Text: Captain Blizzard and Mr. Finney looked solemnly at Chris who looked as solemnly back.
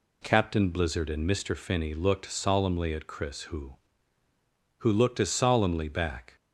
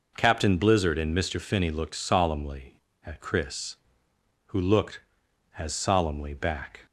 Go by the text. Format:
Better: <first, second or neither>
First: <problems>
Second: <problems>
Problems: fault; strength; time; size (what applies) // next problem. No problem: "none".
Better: second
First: says "who" twice; at 4.7 s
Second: none